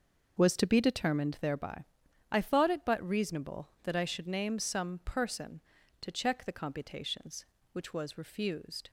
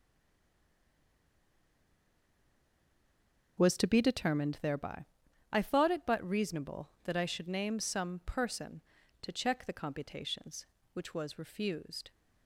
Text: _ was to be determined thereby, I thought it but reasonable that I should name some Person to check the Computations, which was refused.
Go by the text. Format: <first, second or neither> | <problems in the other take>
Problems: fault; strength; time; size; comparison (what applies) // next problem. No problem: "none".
first | stays silent before the first word; strong; until 3.5 s; 3.5 s long // starts louder than the rest; noticeable; until 4.5 s; 6 dB; noticeable in the first